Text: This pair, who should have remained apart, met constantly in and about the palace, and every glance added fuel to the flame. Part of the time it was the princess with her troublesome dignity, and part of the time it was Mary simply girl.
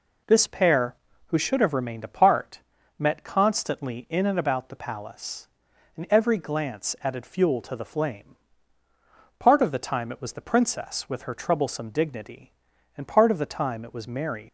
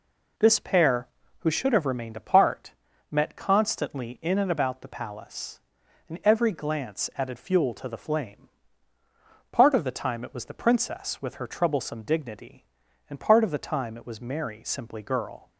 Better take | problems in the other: second | stops before "simply girl"; at 14.4 s

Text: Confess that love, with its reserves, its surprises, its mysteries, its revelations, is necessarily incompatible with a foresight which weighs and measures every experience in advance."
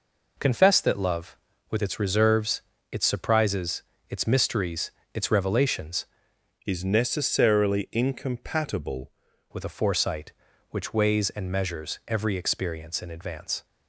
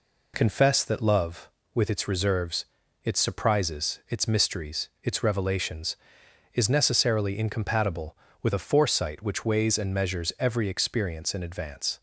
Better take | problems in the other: second | changes voice from "is" to "incompatible"; from 6.6 to 9.1 s; 2.5 s long

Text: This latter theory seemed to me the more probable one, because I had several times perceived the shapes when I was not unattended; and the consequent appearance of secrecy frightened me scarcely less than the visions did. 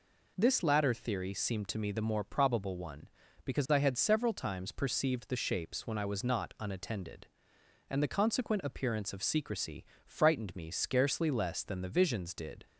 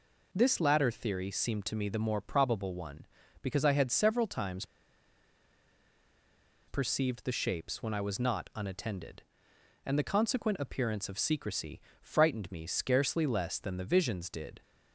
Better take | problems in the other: first | pauses between "times" and "perceived"; strong; at 4.6 s; 2.0 s long // pauses between "secrecy" and "frightened"; slight; at 11.7 s; 0.22 s long; slight in the first

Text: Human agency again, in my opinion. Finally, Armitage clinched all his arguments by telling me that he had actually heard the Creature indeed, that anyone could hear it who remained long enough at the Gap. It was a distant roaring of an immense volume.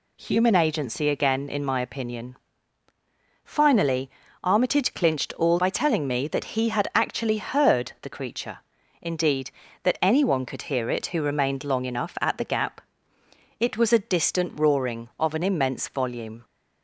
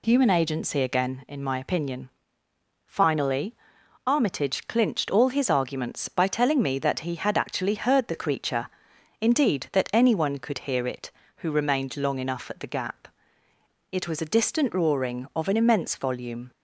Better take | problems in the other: second | skips "his arguments"; at 5.5 s // pauses between "Creature" and "indeed"; at 8.5 s; 0.44 s long; noticeable in the second

